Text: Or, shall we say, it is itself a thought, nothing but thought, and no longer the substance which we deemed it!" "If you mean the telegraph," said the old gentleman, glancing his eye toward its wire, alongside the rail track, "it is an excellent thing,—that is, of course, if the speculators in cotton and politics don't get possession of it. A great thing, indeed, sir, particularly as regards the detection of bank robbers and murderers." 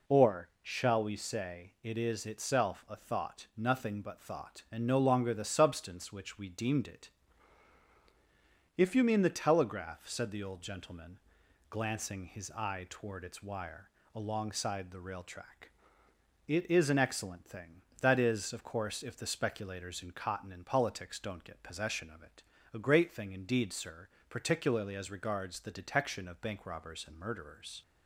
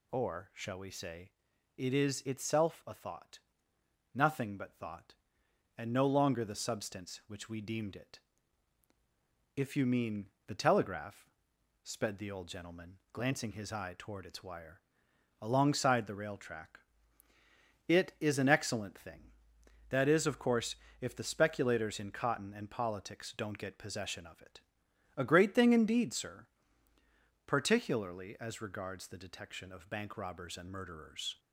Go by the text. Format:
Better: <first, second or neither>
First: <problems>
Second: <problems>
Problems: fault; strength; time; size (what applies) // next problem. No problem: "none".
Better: first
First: none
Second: pauses between "mean" and "the"; slight; at 10.3 s; 0.16 s long // says "sped" for "said"; at 11.8 s